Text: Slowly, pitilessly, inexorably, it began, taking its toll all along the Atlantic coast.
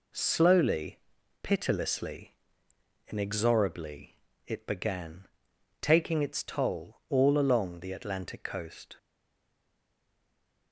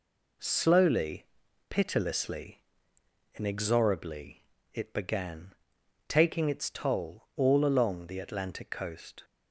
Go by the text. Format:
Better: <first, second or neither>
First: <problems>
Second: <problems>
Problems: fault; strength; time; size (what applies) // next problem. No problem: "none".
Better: second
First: stays silent after the last word; noticeable; from 8.9 s on; 1.8 s long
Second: none